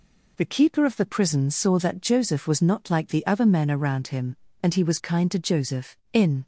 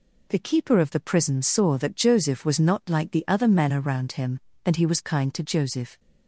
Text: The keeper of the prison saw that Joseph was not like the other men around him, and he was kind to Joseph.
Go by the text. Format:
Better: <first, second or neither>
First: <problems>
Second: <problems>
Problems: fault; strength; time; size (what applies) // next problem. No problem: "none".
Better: second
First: goes on to say "In"; slight; from 6.1 s on; 0.34 s long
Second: none